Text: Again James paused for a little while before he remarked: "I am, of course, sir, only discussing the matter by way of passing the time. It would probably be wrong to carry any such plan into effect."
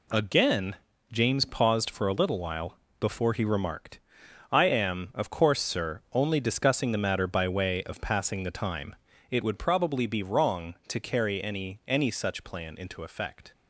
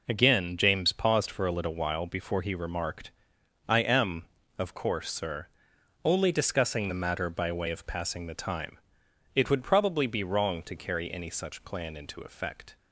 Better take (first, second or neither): second